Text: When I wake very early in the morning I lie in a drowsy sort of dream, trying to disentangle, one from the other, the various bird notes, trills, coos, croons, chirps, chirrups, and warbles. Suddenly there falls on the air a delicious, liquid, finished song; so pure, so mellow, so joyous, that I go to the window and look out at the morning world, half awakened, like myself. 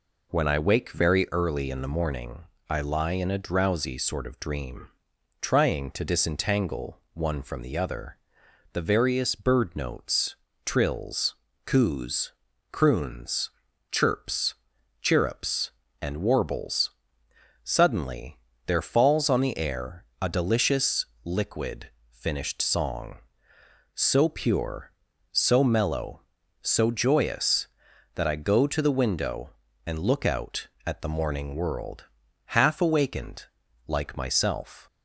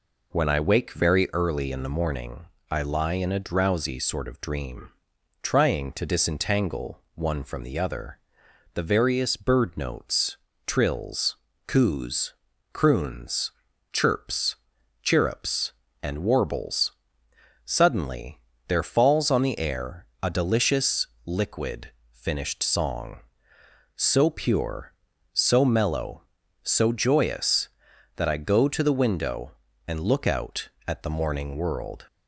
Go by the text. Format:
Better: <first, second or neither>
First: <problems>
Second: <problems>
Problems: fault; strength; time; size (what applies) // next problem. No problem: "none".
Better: first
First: pauses between "morning" and "I"; slight; at 2.4 s; 0.26 s long // pauses between "Suddenly" and "there"; slight; at 18.3 s; 0.30 s long // pauses between "air" and "a"; slight; at 20.0 s; 0.16 s long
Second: pauses between "morning" and "I"; slight; at 2.4 s; 0.26 s long // pauses between "Suddenly" and "there"; slight; at 18.3 s; 0.30 s long // pauses between "air" and "a"; slight; at 20.0 s; 0.16 s long // stops before "half awakened like myself"; at 32.0 s